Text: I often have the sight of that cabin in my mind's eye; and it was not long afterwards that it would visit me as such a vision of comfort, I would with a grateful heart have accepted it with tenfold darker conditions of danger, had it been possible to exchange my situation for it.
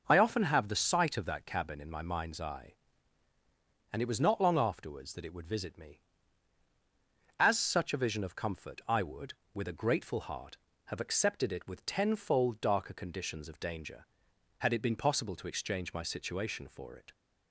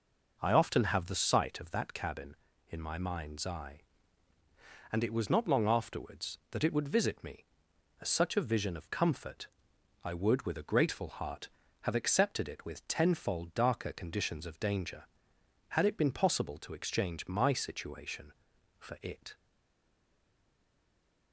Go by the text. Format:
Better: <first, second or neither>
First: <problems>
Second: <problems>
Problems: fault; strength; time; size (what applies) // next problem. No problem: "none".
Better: first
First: none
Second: stays silent after the last word; noticeable; from 19.3 s on; 2.0 s long